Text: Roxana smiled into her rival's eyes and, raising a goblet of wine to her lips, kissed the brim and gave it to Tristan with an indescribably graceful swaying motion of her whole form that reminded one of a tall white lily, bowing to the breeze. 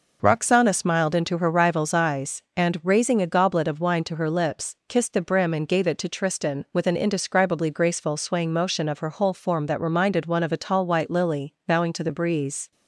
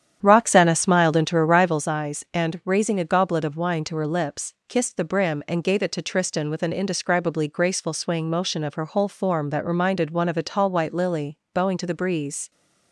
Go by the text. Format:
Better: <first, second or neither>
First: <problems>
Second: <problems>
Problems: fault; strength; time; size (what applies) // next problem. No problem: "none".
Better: first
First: none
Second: starts louder than the rest; strong; until 1.8 s; 9 dB